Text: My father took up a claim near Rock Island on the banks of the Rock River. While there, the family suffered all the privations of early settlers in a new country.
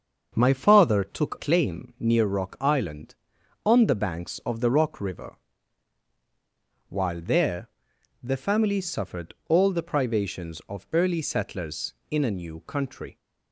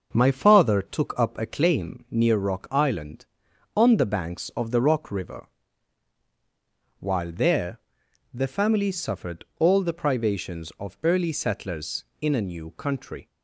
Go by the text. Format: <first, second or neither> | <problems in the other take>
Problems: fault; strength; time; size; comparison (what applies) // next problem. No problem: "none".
second | starts louder than the rest; until 1.3 s; 6.5 dB // skips "up a"; at 1.3 s